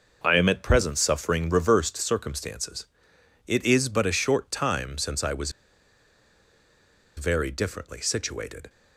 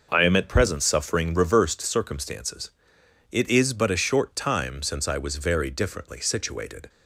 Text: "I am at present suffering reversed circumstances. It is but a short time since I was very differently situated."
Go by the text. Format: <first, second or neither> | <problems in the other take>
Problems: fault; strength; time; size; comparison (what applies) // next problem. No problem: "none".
second | pauses between "was" and "very"; strong; at 5.5 s; 1.6 s long